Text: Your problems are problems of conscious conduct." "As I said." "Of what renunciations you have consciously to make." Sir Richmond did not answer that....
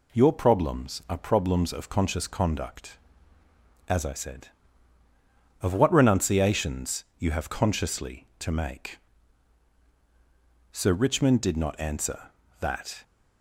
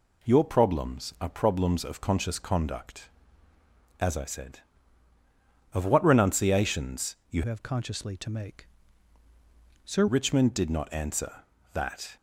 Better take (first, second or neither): first